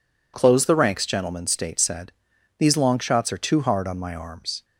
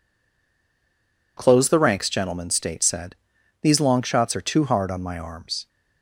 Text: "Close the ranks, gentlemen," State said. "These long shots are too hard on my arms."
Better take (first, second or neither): first